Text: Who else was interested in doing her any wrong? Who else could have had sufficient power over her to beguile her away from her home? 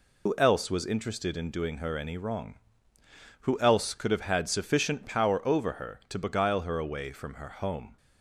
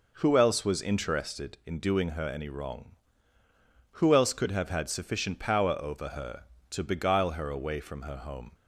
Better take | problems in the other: second | loses the start of "Who"; at 0.2 s; 70 ms

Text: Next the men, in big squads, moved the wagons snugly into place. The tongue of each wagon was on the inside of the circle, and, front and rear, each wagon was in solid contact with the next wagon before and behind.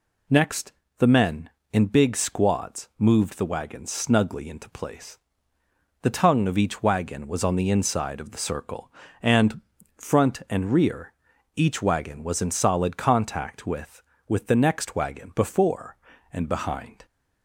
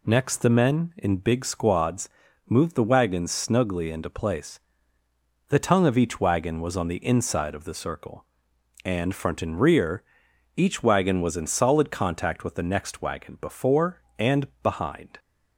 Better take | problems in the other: second | pauses between "Next" and "the"; slight; at 0.7 s; 0.26 s long // says "with" twice; at 14.2 s

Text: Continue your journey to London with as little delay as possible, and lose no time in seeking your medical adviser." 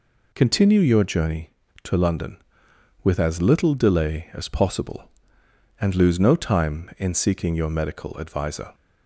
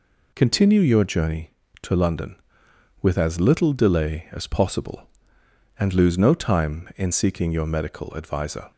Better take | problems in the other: neither | none

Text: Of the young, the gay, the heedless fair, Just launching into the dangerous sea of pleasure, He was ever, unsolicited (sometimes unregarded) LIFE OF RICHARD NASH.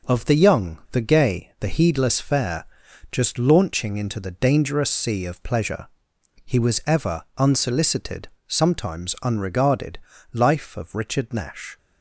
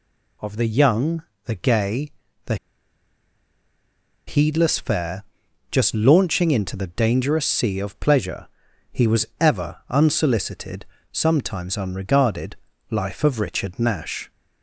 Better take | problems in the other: first | pauses between "the" and "heedless"; strong; at 2.5 s; 1.7 s long

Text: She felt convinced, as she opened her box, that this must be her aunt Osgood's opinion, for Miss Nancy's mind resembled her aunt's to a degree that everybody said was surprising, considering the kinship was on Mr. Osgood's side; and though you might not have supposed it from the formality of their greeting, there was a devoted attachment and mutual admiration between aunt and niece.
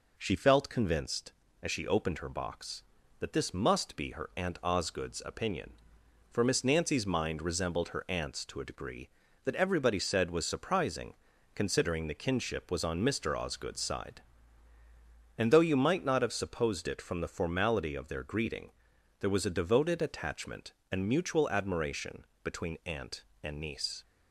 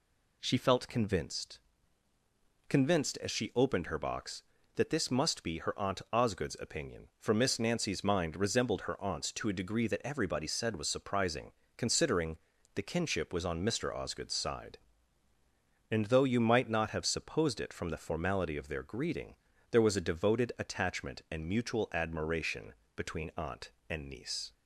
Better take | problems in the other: first | says "convinced" twice; at 2.6 s // pauses between "considering" and "the"; at 12.3 s; 0.38 s long // pauses between "admiration" and "between"; slight; at 22.7 s; 0.22 s long; slight in the first

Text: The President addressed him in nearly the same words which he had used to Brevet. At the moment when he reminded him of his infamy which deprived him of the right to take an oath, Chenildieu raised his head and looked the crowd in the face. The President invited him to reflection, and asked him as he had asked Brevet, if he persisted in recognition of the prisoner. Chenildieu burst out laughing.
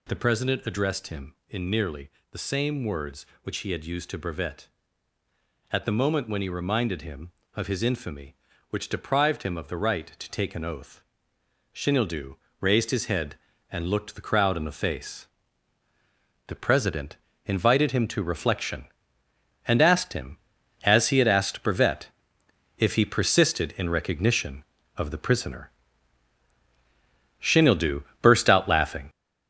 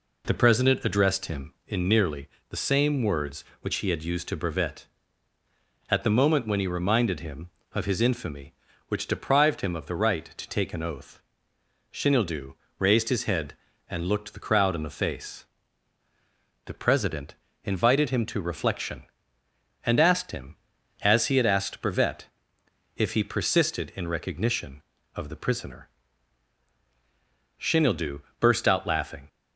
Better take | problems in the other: second | gets louder; throughout; 7 dB // pauses between "nearly" and "the"; slight; at 2.0 s; 0.22 s long; slight in the second // pauses between "Chenildieu" and "raised"; slight; at 12.3 s; 0.26 s long; slight in the second // pauses between "President" and "invited"; slight; at 17.1 s; 0.28 s long; slight in the second // pauses between "Chenildieu" and "burst"; slight; at 28.0 s; 0.18 s long; slight in the second

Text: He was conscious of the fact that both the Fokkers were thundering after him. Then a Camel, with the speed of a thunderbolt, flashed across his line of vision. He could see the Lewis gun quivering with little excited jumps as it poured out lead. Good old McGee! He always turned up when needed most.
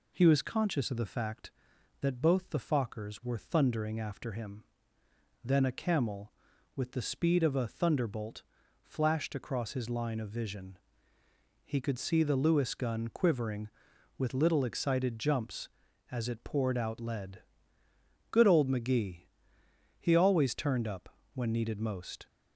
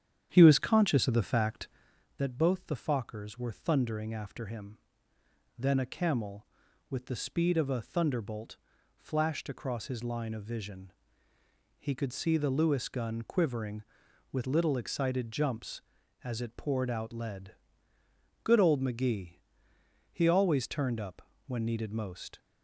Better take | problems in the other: first | starts louder than the rest; strong; until 1.9 s; 9 dB // pauses between "up" and "when"; slight; at 21.2 s; 0.24 s long; slight in the first

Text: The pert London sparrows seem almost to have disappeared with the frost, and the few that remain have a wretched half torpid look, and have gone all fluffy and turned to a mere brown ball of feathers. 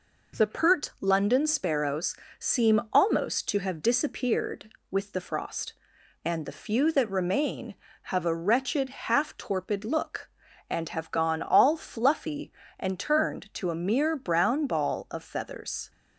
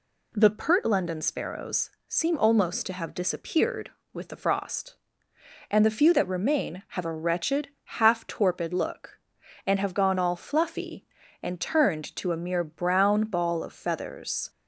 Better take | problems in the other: neither | pauses between "sparrows" and "seem"; slight; the same in both // pauses between "wretched" and "half"; slight; the same in both

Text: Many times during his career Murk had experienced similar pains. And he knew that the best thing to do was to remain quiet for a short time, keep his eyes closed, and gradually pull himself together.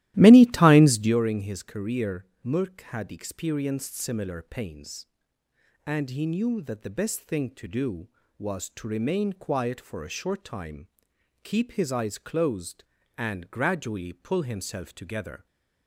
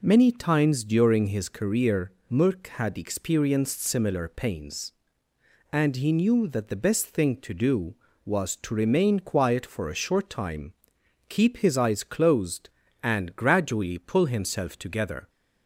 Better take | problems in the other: second | starts louder than the rest; strong; until 1.2 s; 15 dB // pauses between "career" and "Murk"; slight; at 2.2 s; 0.18 s long; slight in the second // stays silent after the last word; slight; from 15.3 s on; 0.5 s long

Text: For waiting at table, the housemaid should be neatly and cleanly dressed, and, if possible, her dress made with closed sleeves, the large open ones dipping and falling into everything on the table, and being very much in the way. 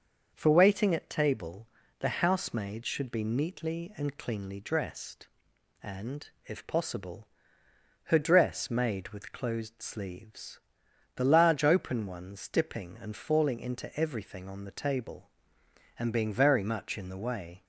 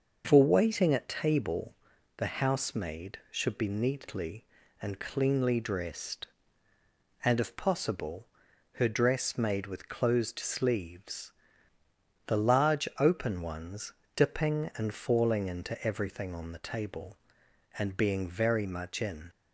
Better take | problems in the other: first | starts louder than the rest; noticeable; until 1.2 s; 6 dB; also in the first // pauses between "ones" and "dipping"; slight; at 13.9 s; 0.24 s long // stops before "the way"; at 19.2 s

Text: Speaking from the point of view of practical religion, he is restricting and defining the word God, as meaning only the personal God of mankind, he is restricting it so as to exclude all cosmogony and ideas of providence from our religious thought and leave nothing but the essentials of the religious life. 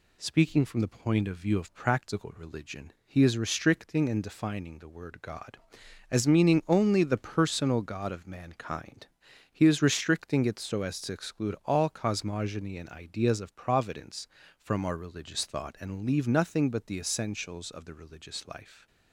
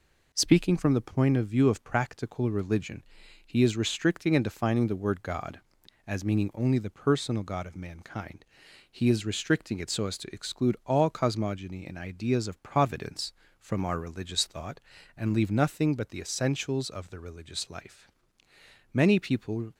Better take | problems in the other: first | goes on to say "Many people"; noticeable; from 18.9 s on; 0.80 s long

